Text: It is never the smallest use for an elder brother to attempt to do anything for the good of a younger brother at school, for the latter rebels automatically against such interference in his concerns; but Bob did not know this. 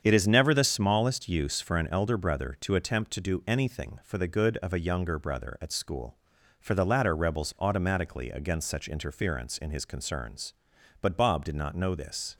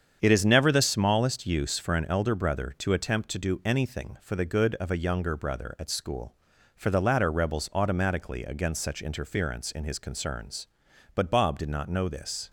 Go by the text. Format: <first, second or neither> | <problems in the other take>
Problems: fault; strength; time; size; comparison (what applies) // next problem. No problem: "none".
neither | starts louder than the rest; strong; the same in both